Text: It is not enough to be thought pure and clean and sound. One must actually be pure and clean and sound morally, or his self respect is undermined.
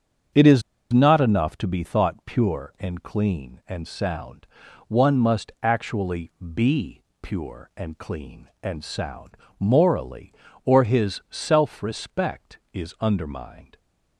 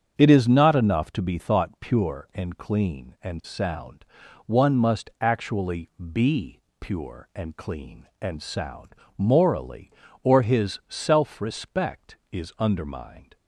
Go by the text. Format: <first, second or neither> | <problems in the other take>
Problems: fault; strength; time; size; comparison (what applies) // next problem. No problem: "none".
second | starts louder than the rest; strong; until 1.6 s; 7.5 dB; strong in the second // pauses between "is" and "not"; slight; at 0.6 s; 0.31 s long // pauses between "actually" and "be"; slight; at 6.2 s; 0.24 s long; slight in the second // pauses between "be" and "pure"; slight; at 7.0 s; 0.20 s long; slight in the second // pauses between "sound" and "morally"; slight; at 9.3 s; 0.22 s long; slight in the second